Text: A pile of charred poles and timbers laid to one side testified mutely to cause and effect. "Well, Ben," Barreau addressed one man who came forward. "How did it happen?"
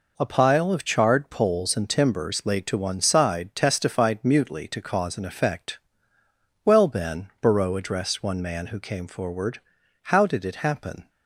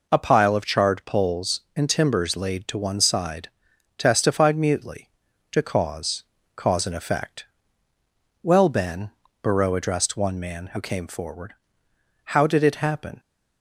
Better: first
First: none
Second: pauses between "side" and "testified"; noticeable; at 3.4 s; 0.48 s long // says "cause" twice; at 6.5 s

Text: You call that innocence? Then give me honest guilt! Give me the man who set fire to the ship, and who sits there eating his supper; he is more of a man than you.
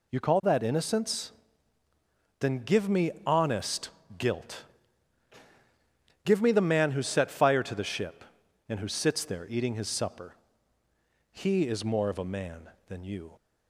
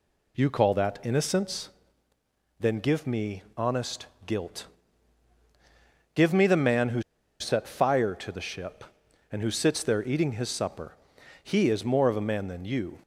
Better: first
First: pauses between "honest" and "guilt"; slight; at 3.8 s; 0.28 s long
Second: pauses between "honest" and "guilt"; slight; at 4.0 s; 0.20 s long // pauses between "who" and "set"; at 7.0 s; 0.38 s long

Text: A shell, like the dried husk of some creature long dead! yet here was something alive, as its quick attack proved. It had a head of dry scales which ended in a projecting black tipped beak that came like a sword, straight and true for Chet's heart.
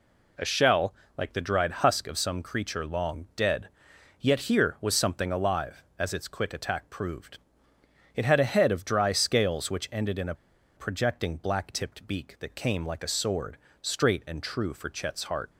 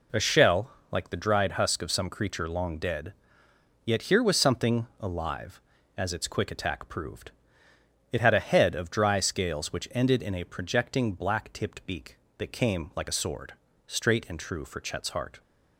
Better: second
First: pauses between "a" and "projecting"; at 10.3 s; 0.42 s long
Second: none

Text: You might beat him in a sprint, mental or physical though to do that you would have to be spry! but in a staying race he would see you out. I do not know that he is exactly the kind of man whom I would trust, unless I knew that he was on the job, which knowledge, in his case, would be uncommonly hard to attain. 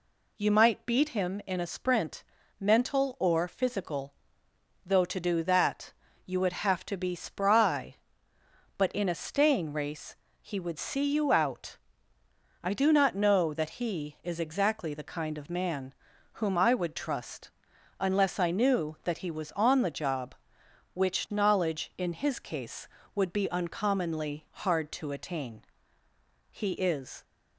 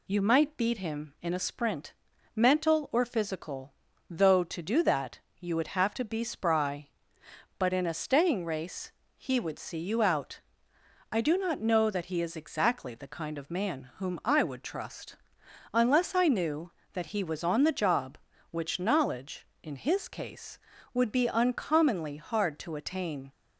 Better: second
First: pauses between "physical" and "though"; noticeable; at 4.1 s; 0.72 s long // pauses between "that" and "you"; slight; at 5.9 s; 0.34 s long // pauses between "race" and "he"; slight; at 10.1 s; 0.26 s long // pauses between "man" and "whom"; at 15.9 s; 0.38 s long // goes on to say "He is"; noticeable; from 26.5 s on; 0.72 s long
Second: pauses between "physical" and "though"; slight; at 3.7 s; 0.36 s long // pauses between "that" and "you"; slight; at 5.1 s; 0.22 s long // pauses between "race" and "he"; slight; at 8.9 s; 0.26 s long

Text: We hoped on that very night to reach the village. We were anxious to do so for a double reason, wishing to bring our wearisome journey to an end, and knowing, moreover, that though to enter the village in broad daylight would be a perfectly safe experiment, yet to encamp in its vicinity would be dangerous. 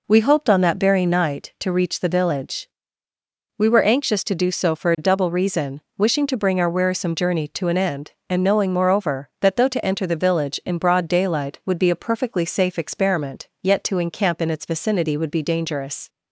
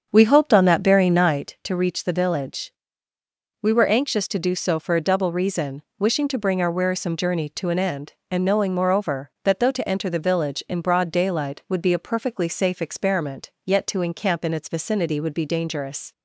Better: first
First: none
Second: starts louder than the rest; strong; until 1.6 s; 7.5 dB

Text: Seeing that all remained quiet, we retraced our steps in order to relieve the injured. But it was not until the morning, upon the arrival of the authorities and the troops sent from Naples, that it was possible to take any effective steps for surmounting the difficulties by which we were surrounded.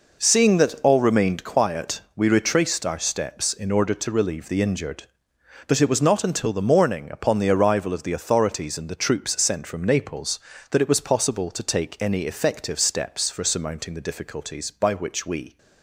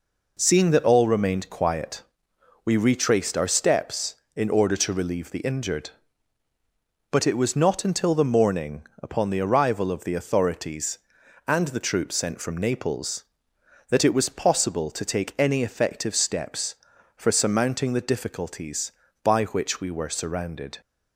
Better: second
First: stops before "were surrounded"; at 15.5 s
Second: none

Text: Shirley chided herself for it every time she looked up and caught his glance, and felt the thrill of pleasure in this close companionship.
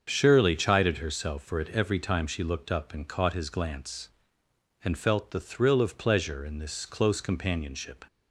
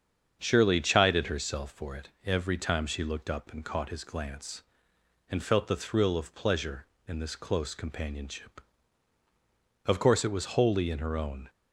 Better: first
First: starts louder than the rest; until 1.0 s; 7 dB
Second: starts louder than the rest; strong; until 1.4 s; 7 dB // goes on to say "Of course it was wholly in her own"; from 9.8 s on; 1.6 s long

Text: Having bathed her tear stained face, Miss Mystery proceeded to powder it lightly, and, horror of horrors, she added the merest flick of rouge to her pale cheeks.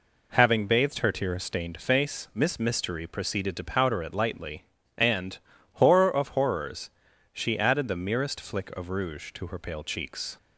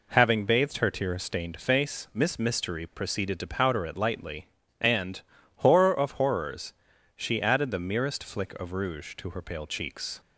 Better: neither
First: none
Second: none

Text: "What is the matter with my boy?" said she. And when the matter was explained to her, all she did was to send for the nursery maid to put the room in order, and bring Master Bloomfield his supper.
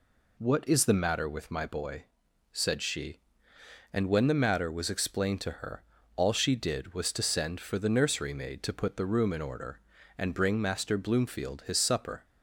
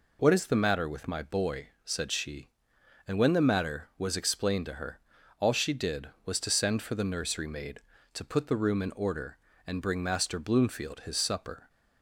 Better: neither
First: none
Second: none

